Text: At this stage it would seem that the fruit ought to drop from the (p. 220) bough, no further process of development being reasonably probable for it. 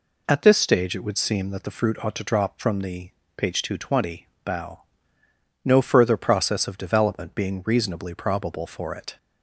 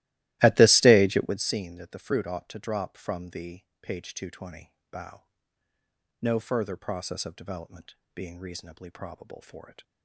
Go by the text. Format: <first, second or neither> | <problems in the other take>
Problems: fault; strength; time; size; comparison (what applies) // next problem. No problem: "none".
first | starts louder than the rest; strong; until 1.5 s; 17 dB // pauses between "development" and "being"; slight; at 7.9 s; 0.18 s long